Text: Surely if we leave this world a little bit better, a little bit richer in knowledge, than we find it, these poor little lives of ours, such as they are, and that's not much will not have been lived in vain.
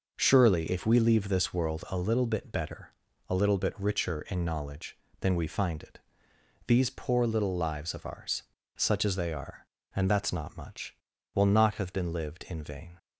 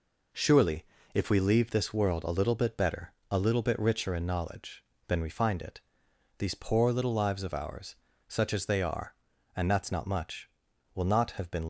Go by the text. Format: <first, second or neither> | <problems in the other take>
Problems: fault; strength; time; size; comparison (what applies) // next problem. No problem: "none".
first | pauses between "Surely" and "if"; slight; at 0.8 s; 0.30 s long // stops before "lived in vain"; at 11.6 s